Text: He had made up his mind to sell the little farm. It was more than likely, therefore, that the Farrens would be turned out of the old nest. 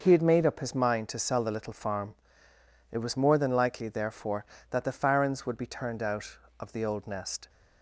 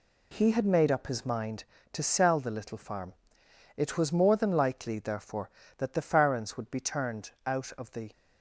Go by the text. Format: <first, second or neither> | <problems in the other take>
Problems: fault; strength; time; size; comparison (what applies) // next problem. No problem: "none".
first | pauses between "turned" and "out"; slight; at 7.3 s; 0.16 s long // stops before "old nest"; at 8.1 s